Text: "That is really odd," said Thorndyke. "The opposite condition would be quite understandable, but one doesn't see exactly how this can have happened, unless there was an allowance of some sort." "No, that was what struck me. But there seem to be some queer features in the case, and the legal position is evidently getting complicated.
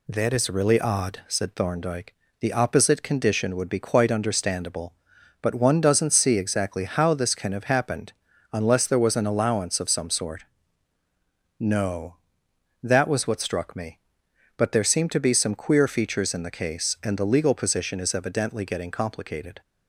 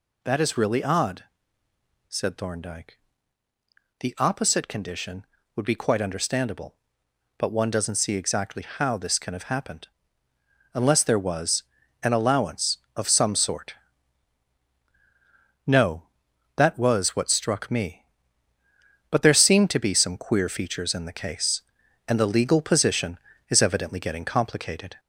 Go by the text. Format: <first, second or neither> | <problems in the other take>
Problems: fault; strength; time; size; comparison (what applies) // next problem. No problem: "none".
first | gets louder; slight; throughout; 2 dB // pauses between "was" and "an"; at 11.6 s; 0.40 s long